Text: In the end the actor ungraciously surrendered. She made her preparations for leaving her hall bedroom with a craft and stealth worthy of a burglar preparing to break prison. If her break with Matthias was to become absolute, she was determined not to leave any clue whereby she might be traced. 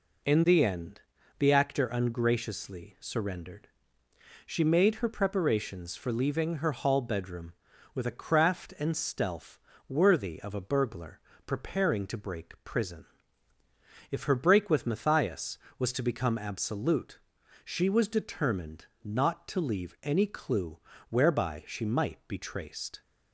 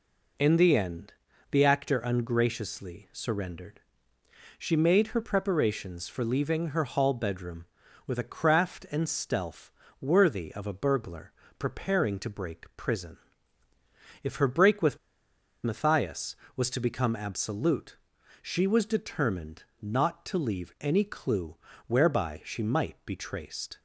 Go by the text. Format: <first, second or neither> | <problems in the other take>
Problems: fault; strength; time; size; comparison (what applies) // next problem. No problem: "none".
first | pauses between "end" and "the"; at 1.1 s; 0.38 s long; also in the first // pauses between "stealth" and "worthy"; slight; at 9.7 s; 0.30 s long; slight in the first // pauses between "burglar" and "preparing"; slight; at 11.3 s; 0.26 s long; slight in the first // pauses between "with" and "Matthias"; noticeable; at 14.9 s; 0.66 s long // pauses between "determined" and "not"; slight; at 19.6 s; 0.18 s long; slight in the first // pauses between "clue" and "whereby"; slight; at 21.5 s; 0.30 s long; slight in the first